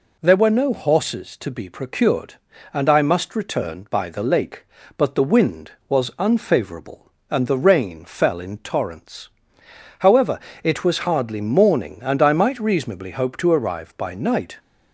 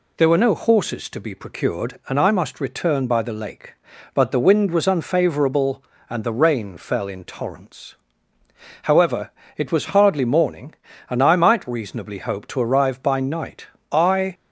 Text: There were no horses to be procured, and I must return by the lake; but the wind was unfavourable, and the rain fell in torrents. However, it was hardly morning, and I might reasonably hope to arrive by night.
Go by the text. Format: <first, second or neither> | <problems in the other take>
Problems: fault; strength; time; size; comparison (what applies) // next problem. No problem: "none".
first | goes on to say "I"; slight; from 13.9 s on; 0.42 s long